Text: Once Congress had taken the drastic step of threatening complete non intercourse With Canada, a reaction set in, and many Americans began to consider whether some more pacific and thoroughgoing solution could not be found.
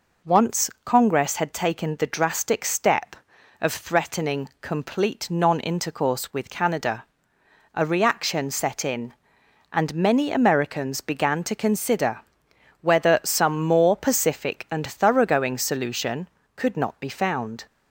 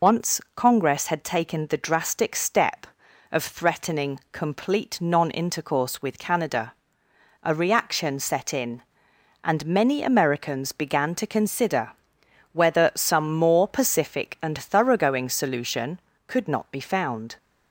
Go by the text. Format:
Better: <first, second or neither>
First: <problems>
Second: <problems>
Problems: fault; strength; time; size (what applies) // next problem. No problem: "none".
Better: first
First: pauses between "Once" and "Congress"; slight; at 0.6 s; 0.16 s long // pauses between "consider" and "whether"; noticeable; at 12.2 s; 0.60 s long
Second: loses the start of "Once"; at 0.0 s; 70 ms // pauses between "Once" and "Congress"; slight; at 0.3 s; 0.16 s long // pauses between "consider" and "whether"; noticeable; at 11.9 s; 0.60 s long